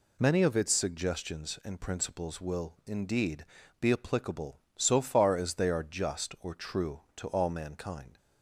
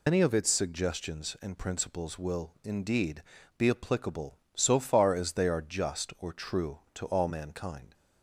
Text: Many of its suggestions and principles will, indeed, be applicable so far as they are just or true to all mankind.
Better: first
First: none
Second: loses the start of "Many"; at 0.0 s; 90 ms

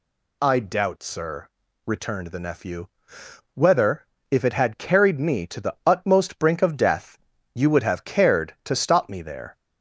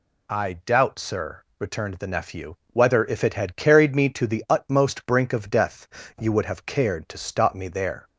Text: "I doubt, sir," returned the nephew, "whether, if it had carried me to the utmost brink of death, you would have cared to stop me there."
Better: neither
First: none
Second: none

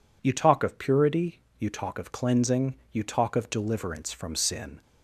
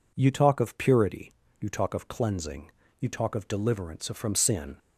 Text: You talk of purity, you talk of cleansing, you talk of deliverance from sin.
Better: neither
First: none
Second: none

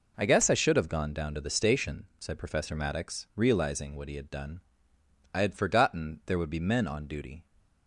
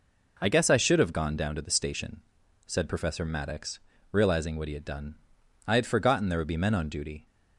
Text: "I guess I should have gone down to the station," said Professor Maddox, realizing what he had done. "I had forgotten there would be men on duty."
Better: neither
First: none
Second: none

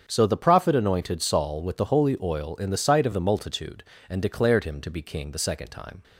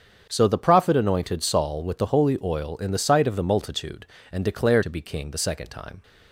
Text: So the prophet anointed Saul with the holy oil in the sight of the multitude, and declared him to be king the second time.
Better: first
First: starts louder than the rest; strong; until 1.0 s; 7.5 dB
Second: starts louder than the rest; strong; until 1.3 s; 7.5 dB // skips "him"; at 4.8 s

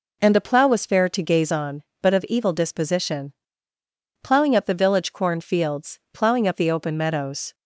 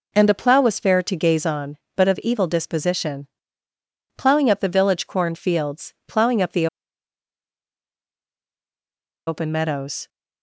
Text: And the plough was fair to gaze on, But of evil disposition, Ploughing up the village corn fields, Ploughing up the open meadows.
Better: first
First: none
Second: pauses between "the" and "open"; strong; at 6.6 s; 2.6 s long

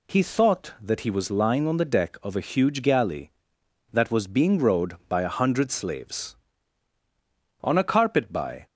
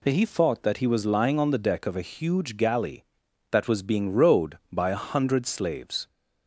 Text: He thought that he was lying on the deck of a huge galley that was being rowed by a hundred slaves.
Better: second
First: goes on to say "On a carpet by"; noticeable; from 7.6 s on; 1.0 s long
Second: none

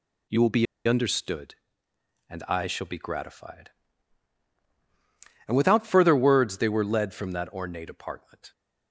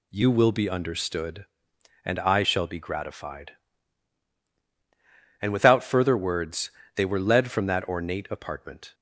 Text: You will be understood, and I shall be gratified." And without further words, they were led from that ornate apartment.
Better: second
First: pauses between "be" and "understood"; slight; at 0.6 s; 0.22 s long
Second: none

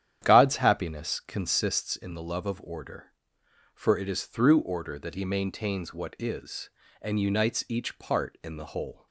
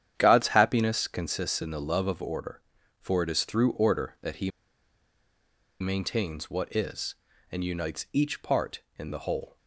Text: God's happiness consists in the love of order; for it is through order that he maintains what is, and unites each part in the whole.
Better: first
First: starts louder than the rest; strong; until 1.2 s; 10 dB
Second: starts louder than the rest; strong; until 1.1 s; 9.5 dB // pauses between "he" and "maintains"; strong; at 4.5 s; 1.3 s long

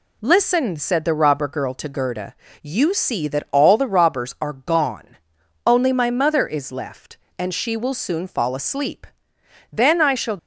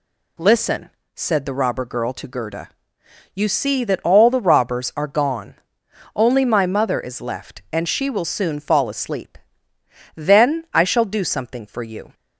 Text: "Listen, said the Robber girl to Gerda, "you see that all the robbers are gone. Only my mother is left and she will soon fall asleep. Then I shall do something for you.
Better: second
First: stops before "do something for you"; at 10.3 s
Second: none

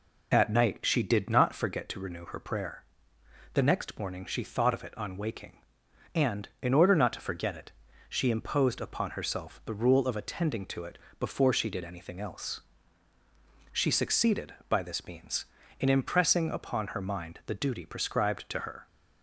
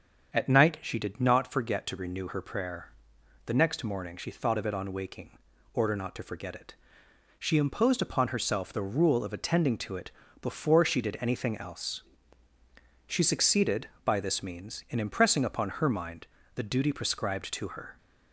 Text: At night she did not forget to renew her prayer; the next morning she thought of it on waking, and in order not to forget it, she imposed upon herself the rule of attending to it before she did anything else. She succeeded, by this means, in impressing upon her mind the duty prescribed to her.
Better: first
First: pauses between "it" and "before"; slight; at 10.9 s; 0.22 s long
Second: starts louder than the rest; strong; until 1.3 s; 7 dB // skips "and in"; at 5.5 s // pauses between "it" and "before"; slight; at 10.1 s; 0.30 s long // pauses between "mind" and "the"; slight; at 16.2 s; 0.28 s long

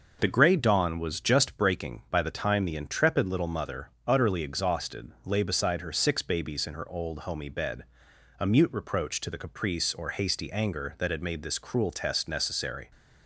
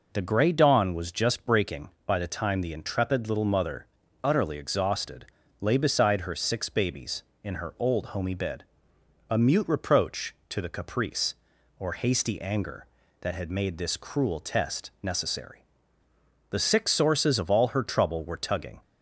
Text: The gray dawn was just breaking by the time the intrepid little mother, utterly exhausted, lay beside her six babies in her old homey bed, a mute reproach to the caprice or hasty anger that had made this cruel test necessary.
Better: first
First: none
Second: goes on to say "The six sources of all her trouble were tugging"; strong; from 16.5 s on; 2.3 s long

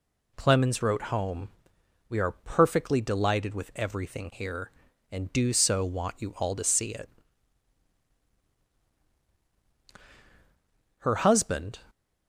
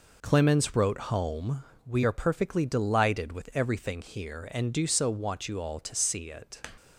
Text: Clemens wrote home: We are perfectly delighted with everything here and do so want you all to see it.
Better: second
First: goes on to say "Her husband"; noticeable; from 10.9 s on; 0.84 s long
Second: none

